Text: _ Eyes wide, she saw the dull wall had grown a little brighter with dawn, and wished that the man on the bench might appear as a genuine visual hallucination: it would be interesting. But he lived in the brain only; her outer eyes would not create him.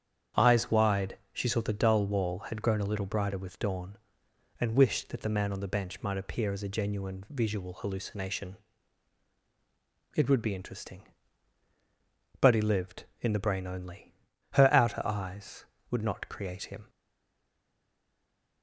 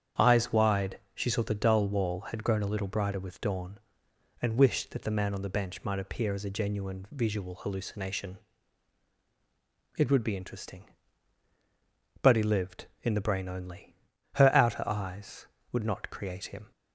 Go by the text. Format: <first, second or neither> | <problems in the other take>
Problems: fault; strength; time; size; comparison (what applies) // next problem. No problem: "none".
second | starts louder than the rest; strong; until 1.5 s; 8 dB; strong in the second // stays silent after the last word; noticeable; from 16.8 s on; 1.8 s long